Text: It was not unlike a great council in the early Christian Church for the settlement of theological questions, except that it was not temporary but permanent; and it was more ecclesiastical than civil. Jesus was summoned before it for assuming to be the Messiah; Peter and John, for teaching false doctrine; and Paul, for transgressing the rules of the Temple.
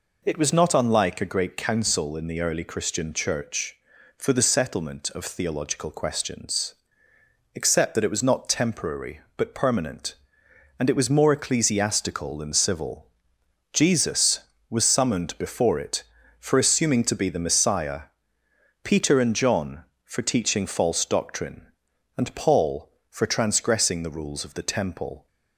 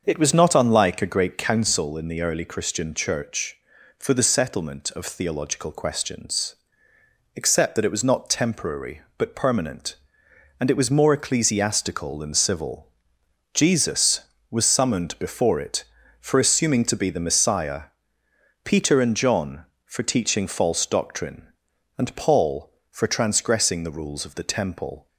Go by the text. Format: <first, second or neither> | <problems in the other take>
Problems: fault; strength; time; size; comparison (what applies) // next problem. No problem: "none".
first | starts louder than the rest; until 1.8 s; 6.5 dB